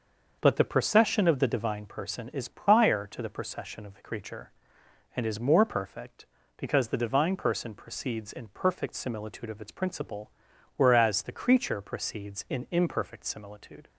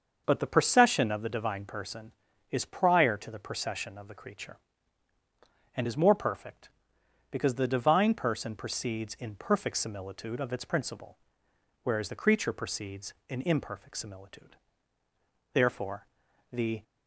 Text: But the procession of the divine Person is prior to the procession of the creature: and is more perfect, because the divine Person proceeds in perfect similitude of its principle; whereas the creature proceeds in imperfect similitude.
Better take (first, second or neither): first